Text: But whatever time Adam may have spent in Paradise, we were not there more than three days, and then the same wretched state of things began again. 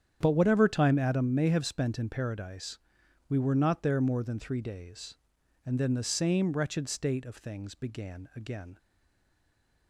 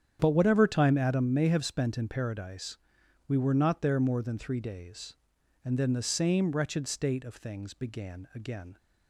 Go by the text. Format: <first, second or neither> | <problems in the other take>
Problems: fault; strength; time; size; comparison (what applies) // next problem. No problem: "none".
second | starts louder than the rest; strong; until 1.2 s; 9 dB; strong in the second // stays silent after the last word; from 8.7 s on; 1.1 s long